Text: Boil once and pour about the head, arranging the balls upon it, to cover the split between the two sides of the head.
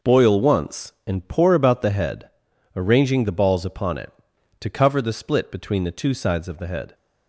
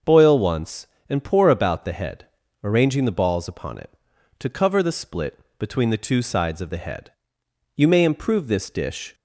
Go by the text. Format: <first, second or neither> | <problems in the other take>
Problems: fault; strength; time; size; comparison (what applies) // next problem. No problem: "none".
first | starts louder than the rest; until 1.2 s; 6 dB // pauses between "split" and "between"; slight; at 5.3 s; 0.20 s long // goes on to say "You may improve this dish"; from 7.7 s on; 1.3 s long